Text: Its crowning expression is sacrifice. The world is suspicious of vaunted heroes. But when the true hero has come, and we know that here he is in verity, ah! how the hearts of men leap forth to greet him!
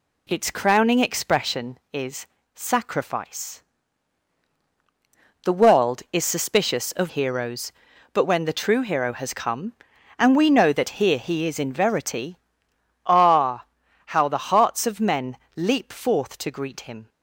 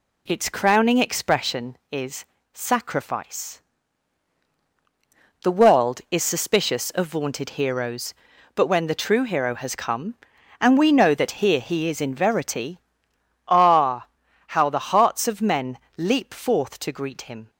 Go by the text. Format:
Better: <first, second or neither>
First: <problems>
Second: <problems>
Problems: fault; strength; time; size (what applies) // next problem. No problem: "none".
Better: second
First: pauses between "is" and "sacrifice"; slight; at 2.2 s; 0.28 s long // skips "vaunted"; at 7.0 s // pauses between "men" and "leap"; slight; at 15.3 s; 0.18 s long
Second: pauses between "is" and "sacrifice"; slight; at 2.2 s; 0.28 s long // pauses between "men" and "leap"; slight; at 15.7 s; 0.18 s long